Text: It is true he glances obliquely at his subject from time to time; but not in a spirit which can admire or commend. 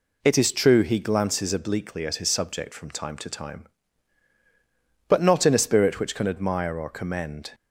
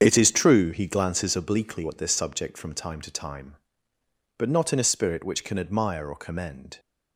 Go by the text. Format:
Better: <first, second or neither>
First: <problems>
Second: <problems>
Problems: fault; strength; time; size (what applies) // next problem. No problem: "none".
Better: first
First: none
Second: starts louder than the rest; strong; until 1.0 s; 7.5 dB // says "this" for "his"; at 1.9 s